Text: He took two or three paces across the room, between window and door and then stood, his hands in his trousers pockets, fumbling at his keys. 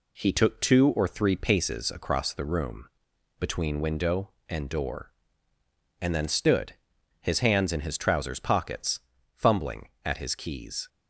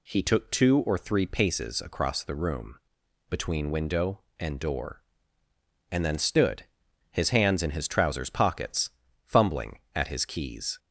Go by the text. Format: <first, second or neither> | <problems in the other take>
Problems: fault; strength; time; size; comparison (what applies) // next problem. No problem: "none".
second | gets quieter; slight; throughout; 3 dB